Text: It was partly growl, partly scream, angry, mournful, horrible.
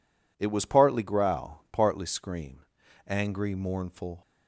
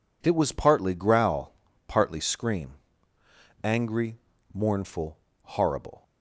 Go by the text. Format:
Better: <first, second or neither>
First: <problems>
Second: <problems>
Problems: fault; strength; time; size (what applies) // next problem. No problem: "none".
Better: second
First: stops before "horrible"; at 4.2 s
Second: none